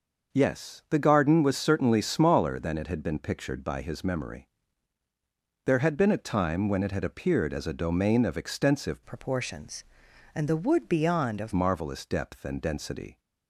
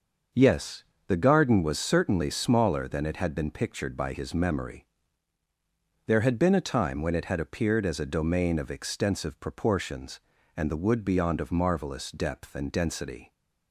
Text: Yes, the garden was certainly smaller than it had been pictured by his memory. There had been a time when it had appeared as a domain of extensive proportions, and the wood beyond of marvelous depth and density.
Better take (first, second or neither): second